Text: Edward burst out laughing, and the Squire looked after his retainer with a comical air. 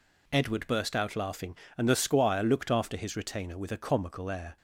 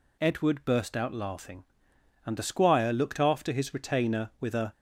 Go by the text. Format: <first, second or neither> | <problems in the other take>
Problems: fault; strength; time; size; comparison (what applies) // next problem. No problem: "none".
first | stops before "comical air"; at 4.7 s